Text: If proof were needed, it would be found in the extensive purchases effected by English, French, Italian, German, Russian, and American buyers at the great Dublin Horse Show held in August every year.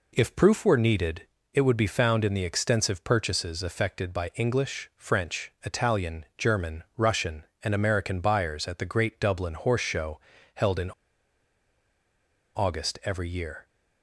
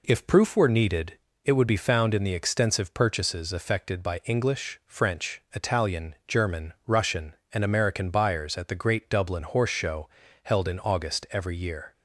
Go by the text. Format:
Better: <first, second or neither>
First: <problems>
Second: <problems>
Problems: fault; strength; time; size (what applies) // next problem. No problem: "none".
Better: second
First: pauses between "Show" and "held"; slight; at 10.1 s; 0.34 s long // pauses between "in" and "August"; strong; at 10.9 s; 1.6 s long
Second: pauses between "Show" and "held"; slight; at 10.0 s; 0.34 s long